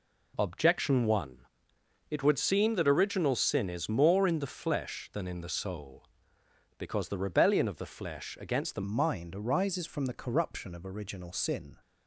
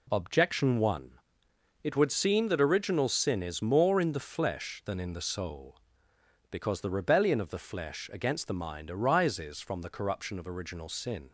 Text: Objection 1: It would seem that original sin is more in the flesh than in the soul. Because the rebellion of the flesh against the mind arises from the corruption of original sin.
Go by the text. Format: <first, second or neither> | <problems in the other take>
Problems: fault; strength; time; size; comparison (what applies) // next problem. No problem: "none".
second | changes voice at "mind"; from 8.8 s on; 2.9 s long